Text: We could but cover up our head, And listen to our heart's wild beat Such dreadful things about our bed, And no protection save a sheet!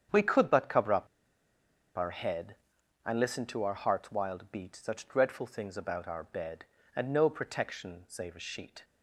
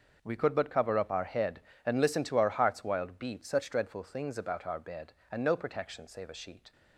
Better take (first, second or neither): second